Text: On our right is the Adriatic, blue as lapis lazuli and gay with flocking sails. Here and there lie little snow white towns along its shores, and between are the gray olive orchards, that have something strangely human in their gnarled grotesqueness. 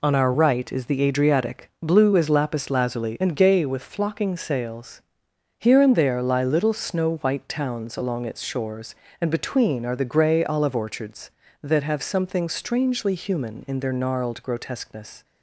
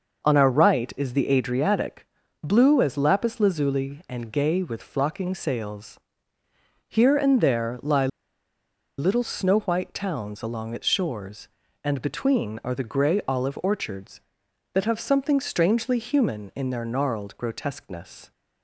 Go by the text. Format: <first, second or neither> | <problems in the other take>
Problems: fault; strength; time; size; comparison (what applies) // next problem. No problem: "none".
first | pauses between "lie" and "little"; noticeable; at 8.0 s; 0.91 s long